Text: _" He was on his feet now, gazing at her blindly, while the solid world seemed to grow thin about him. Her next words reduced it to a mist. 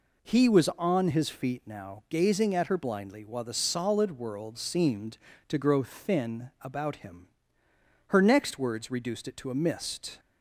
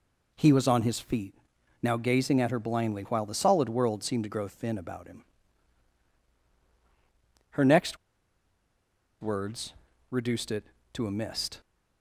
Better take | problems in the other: first | pauses between "feet" and "now"; noticeable; at 1.3 s; 0.46 s long // pauses between "next" and "words"; strong; at 7.9 s; 1.2 s long // pauses between "words" and "reduced"; at 9.7 s; 0.40 s long

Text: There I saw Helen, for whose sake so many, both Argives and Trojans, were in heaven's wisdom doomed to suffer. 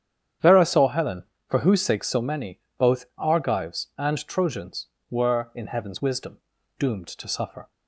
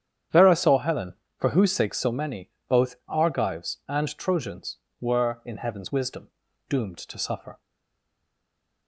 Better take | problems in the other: first | starts louder than the rest; strong; until 1.5 s; 9.5 dB; strong in the first // pauses between "wisdom" and "doomed"; at 6.2 s; 0.40 s long; also in the first // stays silent after the last word; noticeable; from 7.6 s on; 1.2 s long

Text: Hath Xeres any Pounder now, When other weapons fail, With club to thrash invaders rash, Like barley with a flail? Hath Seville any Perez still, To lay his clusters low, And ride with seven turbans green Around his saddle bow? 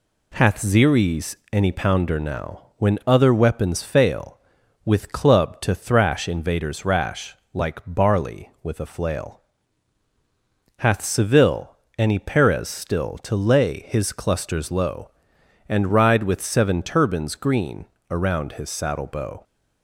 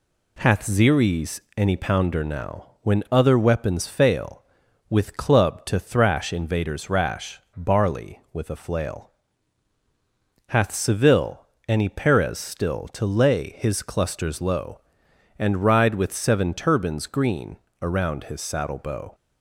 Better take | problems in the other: first | pauses between "Xeres" and "any"; slight; at 1.3 s; 0.18 s long; slight in the first // skips "Like"; at 7.4 s // pauses between "Seville" and "any"; slight; at 11.4 s; 0.22 s long; slight in the first // pauses between "green" and "Around"; slight; at 17.5 s; 0.22 s long; slight in the first

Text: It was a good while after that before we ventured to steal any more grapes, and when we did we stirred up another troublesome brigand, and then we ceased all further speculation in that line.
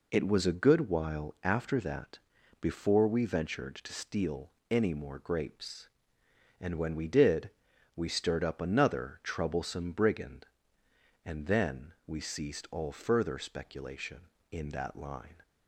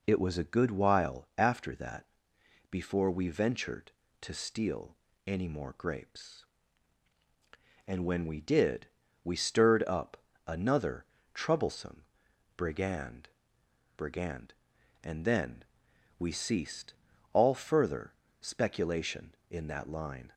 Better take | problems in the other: first | pauses between "that" and "before"; noticeable; at 2.0 s; 0.64 s long; also in the first // pauses between "steal" and "any"; slight; at 4.9 s; 0.30 s long; slight in the first // pauses between "did" and "we"; slight; at 8.8 s; 0.36 s long; noticeable in the first // pauses between "up" and "another"; slight; at 10.1 s; 0.28 s long // pauses between "another" and "troublesome"; slight; at 11.0 s; 0.28 s long // pauses between "troublesome" and "brigand"; noticeable; at 12.0 s; 0.54 s long // says "brigand" twice; at 13.9 s // pauses between "then" and "we"; noticeable; at 15.6 s; 0.56 s long // pauses between "ceased" and "all"; at 16.9 s; 0.38 s long // pauses between "further" and "speculation"; slight; at 18.1 s; 0.30 s long

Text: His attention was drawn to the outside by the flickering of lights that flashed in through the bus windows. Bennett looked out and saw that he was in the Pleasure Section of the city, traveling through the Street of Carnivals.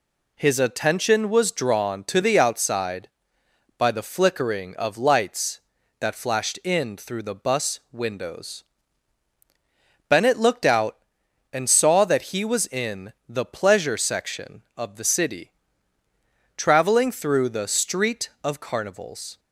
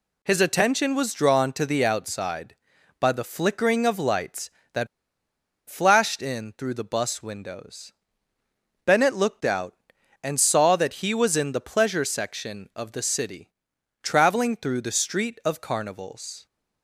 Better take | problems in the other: first | pauses between "that" and "flashed"; noticeable; at 4.8 s; 0.82 s long

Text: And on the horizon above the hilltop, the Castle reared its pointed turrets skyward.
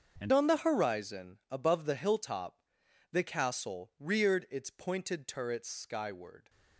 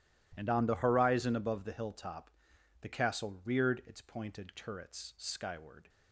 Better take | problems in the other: second | starts louder than the rest; until 1.2 s; 6.5 dB // changes voice at "on"; from 0.3 s on; 6.1 s long

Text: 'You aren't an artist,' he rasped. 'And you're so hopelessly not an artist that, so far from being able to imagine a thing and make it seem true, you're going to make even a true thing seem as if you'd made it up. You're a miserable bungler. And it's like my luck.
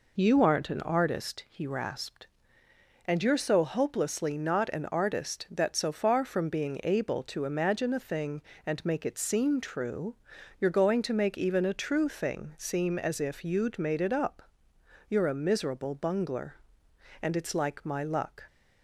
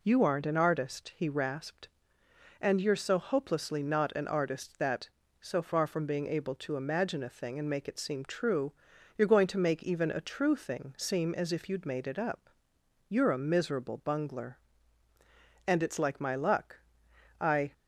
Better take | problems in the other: first | goes on to say "I"; slight; from 17.4 s on; 0.32 s long

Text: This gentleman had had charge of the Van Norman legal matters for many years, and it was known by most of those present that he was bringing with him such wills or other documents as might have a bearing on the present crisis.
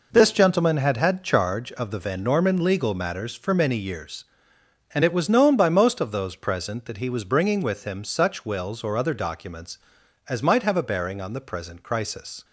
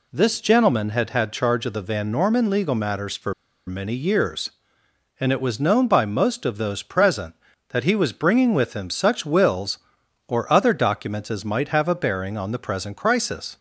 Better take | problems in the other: first | pauses between "for" and "many"; slight; at 3.3 s; 0.33 s long

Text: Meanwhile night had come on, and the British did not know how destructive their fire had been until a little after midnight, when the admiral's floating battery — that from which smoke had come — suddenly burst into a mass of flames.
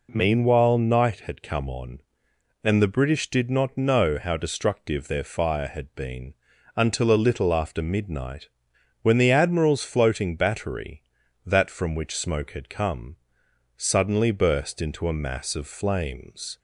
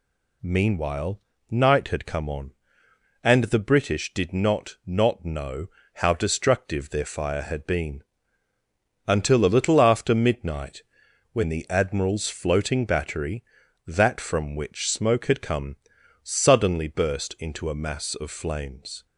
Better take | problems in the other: first | pauses between "Meanwhile" and "night"; slight; at 1.1 s; 0.30 s long // says "not" twice; at 4.8 s // pauses between "know" and "how"; slight; at 5.6 s; 0.30 s long // pauses between "been" and "until"; at 8.0 s; 1.0 s long; also in the first

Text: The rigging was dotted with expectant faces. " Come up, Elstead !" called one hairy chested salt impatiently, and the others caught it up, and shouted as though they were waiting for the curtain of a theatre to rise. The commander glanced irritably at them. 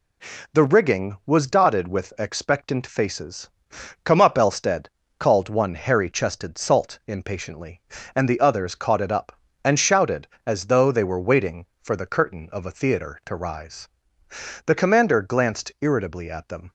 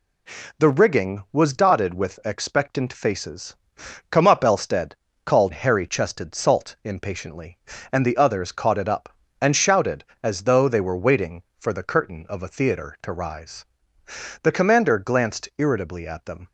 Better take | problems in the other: first | skips "one"; at 5.5 s

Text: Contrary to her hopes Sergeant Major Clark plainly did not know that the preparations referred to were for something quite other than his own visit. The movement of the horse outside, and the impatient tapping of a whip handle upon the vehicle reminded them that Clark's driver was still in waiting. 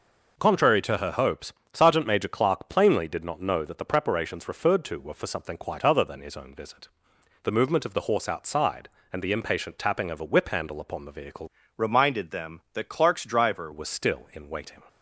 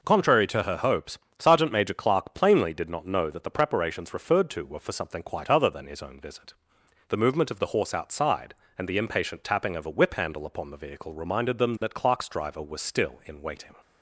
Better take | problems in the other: second | pauses between "hopes" and "Sergeant"; slight; at 1.5 s; 0.18 s long; slight in the second // changes voice from "reminded" to "driver"; from 11.7 to 13.7 s; 2.0 s long

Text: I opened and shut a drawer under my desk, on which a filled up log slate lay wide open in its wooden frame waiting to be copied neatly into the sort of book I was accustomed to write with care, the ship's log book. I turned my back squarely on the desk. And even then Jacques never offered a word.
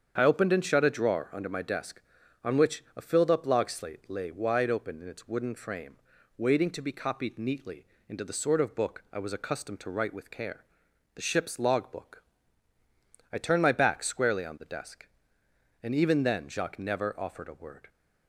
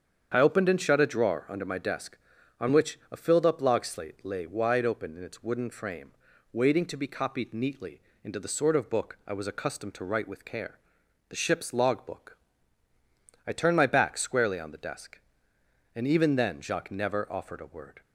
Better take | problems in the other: neither | starts louder than the rest; strong; the same in both // pauses between "frame" and "waiting"; the same in both // pauses between "neatly" and "into"; slight; the same in both

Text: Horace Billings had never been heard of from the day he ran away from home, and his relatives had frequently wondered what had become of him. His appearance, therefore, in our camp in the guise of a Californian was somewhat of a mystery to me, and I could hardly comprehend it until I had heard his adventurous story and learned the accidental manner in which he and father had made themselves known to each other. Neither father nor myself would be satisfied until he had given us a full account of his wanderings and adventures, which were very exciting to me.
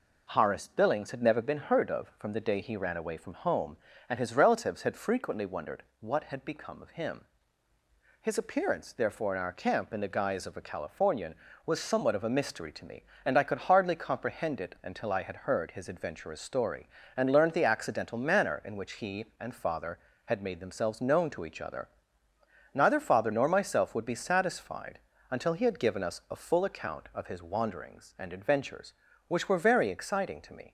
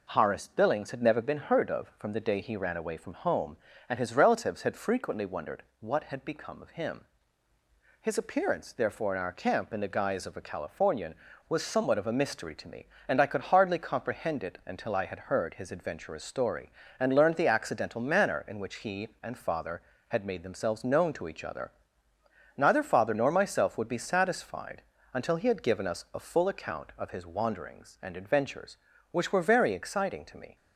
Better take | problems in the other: neither | pauses between "wondered" and "what"; slight; the same in both // pauses between "satisfied" and "until"; slight; the same in both

